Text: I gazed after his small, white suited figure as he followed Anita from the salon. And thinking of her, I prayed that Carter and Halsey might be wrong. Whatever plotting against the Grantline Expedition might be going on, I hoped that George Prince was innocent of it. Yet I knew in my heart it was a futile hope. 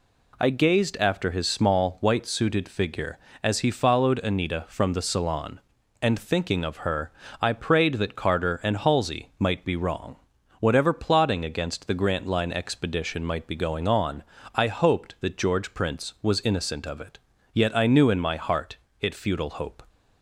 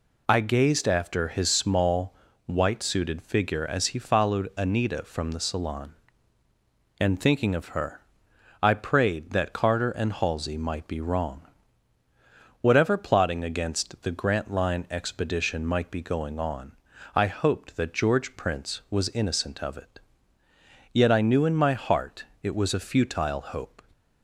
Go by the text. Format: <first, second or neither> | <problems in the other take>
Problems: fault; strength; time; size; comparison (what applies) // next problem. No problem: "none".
second | pauses between "heart" and "it"; slight; at 18.7 s; 0.24 s long; slight in the second // skips "was a"; at 19.1 s